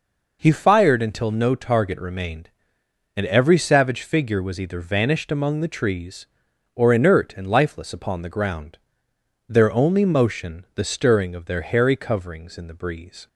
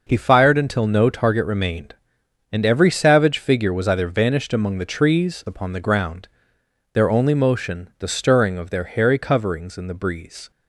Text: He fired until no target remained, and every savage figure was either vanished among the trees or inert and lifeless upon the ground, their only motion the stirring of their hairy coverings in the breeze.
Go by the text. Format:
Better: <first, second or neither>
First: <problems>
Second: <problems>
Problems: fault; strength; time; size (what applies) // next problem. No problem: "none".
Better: first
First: none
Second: skips "or inert and lifeless"; at 5.4 s